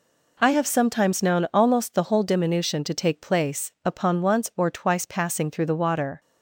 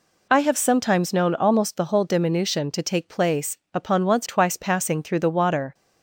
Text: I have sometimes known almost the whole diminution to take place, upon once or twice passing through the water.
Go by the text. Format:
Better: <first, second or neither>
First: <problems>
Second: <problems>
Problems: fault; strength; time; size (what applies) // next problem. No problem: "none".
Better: first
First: none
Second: skips "or"; at 4.2 s